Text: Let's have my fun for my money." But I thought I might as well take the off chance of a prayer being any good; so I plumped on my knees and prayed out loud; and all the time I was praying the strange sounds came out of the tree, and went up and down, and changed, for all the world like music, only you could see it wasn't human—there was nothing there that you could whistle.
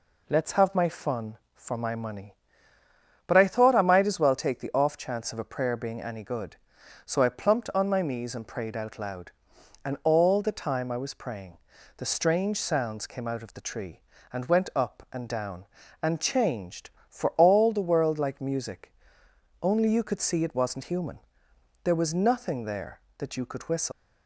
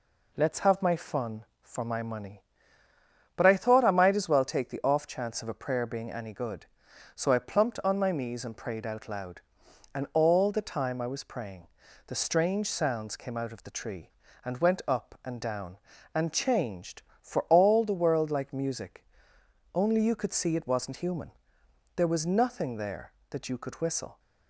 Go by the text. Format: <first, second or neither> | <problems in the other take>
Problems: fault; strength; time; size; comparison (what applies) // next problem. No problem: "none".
second | pauses between "praying" and "the"; at 11.5 s; 0.40 s long; also in the second // leaves "whistle" unfinished; at 23.9 s; 145 ms